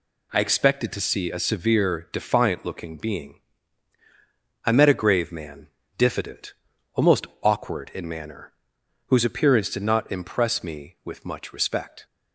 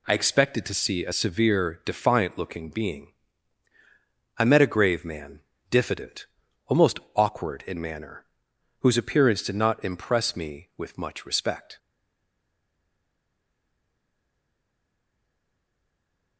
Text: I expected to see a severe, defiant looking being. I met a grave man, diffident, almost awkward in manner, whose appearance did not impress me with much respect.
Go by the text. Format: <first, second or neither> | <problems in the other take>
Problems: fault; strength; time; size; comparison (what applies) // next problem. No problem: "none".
first | pauses between "almost" and "awkward"; slight; at 6.9 s; 0.16 s long; slight in the first // stays silent after the last word; strong; from 11.7 s on; 4.6 s long